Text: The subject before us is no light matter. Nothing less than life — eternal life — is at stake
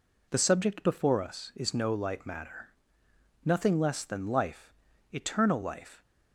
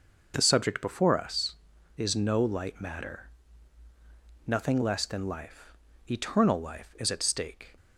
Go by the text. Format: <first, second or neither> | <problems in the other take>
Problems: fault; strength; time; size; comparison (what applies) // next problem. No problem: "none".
second | stops before "is at stake"; at 6.0 s